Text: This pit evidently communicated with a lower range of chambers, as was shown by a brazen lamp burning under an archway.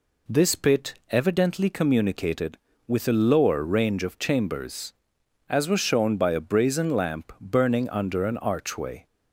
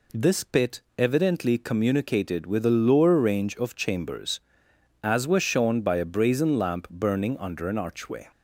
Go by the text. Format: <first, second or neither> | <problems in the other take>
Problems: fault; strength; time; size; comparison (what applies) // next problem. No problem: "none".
neither | pauses between "pit" and "evidently"; slight; the same in both